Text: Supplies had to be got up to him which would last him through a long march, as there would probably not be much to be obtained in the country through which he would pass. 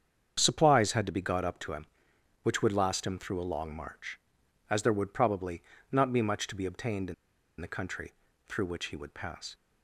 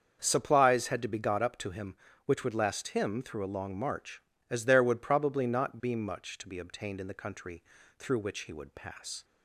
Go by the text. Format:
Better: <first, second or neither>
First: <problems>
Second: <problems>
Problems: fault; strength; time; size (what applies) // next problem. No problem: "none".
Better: second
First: starts louder than the rest; strong; until 1.3 s; 7.5 dB // pauses between "probably" and "not"; slight; at 5.6 s; 0.28 s long // pauses between "in" and "the"; at 7.1 s; 0.45 s long // pauses between "country" and "through"; slight; at 8.1 s; 0.34 s long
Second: starts louder than the rest; until 1.2 s; 7 dB // pauses between "country" and "through"; slight; at 7.6 s; 0.34 s long